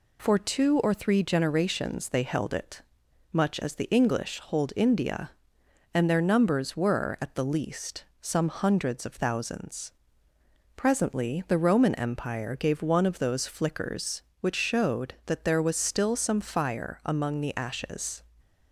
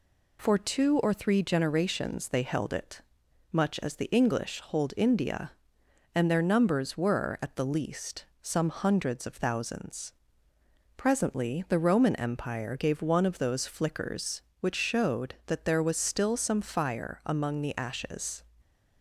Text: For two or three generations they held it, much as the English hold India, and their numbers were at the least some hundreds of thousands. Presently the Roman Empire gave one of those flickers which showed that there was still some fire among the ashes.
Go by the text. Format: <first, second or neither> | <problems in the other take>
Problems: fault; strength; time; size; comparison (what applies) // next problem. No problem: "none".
neither | pauses between "least" and "some"; slight; the same in both